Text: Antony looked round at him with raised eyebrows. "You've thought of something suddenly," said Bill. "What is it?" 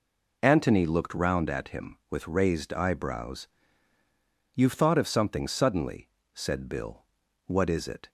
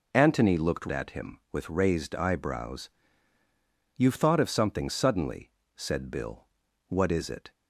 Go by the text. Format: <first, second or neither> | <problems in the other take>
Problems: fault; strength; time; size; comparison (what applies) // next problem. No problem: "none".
first | skips "round"; at 0.8 s